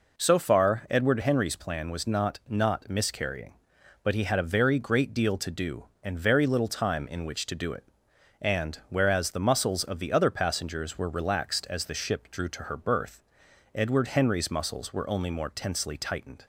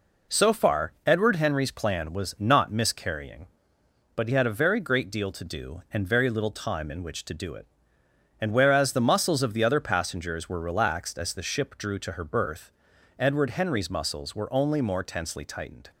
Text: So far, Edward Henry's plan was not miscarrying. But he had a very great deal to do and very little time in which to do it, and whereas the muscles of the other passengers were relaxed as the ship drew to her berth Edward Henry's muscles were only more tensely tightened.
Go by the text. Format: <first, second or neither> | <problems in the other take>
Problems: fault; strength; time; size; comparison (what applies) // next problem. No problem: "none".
second | says "not" twice; at 2.4 s // pauses between "berth" and "Edward"; noticeable; at 13.2 s; 0.50 s long; noticeable in the second